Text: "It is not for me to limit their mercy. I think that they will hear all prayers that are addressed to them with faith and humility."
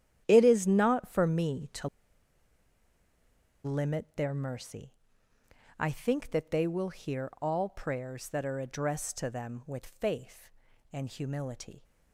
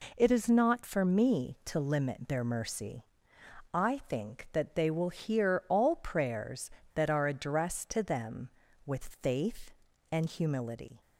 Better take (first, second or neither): second